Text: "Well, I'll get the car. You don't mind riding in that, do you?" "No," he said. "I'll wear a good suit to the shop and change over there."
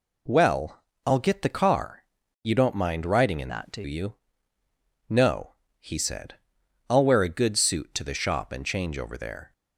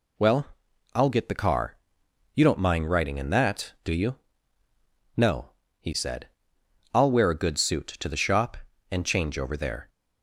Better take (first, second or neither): second